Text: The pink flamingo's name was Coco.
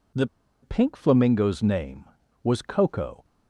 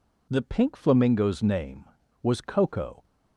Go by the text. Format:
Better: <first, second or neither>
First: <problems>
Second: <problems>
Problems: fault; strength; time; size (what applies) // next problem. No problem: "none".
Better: second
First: pauses between "The" and "pink"; slight; at 0.2 s; 0.35 s long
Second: none